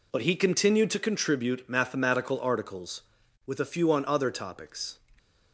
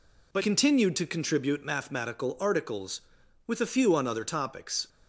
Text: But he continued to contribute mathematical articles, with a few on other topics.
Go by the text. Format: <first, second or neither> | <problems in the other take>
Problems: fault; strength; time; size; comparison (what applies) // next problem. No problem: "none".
first | skips "he"; at 0.4 s